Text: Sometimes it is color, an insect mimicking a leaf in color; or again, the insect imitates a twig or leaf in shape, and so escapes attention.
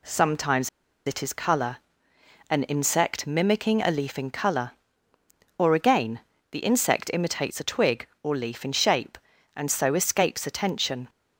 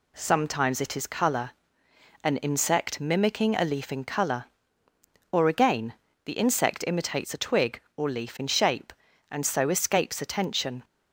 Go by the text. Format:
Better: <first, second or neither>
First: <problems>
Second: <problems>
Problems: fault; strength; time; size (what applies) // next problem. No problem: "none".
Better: second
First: pauses between "Sometimes" and "it"; at 0.6 s; 0.38 s long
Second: none